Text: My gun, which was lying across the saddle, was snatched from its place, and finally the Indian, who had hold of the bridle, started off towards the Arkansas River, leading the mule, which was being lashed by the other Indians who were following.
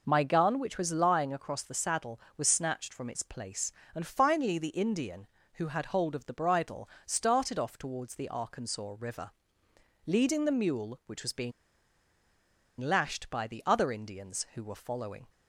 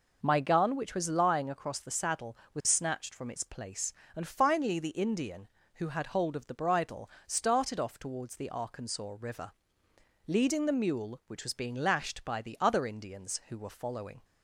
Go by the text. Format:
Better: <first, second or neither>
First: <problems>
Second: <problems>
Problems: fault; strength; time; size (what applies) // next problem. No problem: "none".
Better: second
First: pauses between "being" and "lashed"; strong; at 11.5 s; 1.2 s long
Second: none